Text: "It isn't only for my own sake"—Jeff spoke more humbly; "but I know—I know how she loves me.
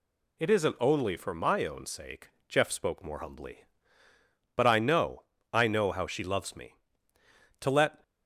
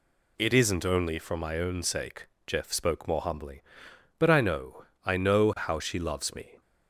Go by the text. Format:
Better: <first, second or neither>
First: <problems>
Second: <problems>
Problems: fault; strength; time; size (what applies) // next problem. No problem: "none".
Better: second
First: goes on to say "To let"; slight; from 7.6 s on; 0.42 s long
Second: none